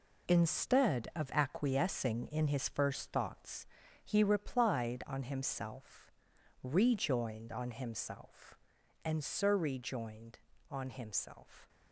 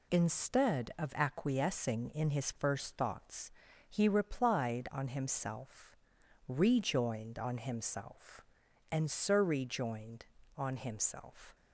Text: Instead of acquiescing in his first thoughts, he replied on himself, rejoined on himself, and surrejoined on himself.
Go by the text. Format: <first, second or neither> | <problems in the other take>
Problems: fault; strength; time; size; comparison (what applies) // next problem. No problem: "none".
second | gets quieter; strong; throughout; 8.5 dB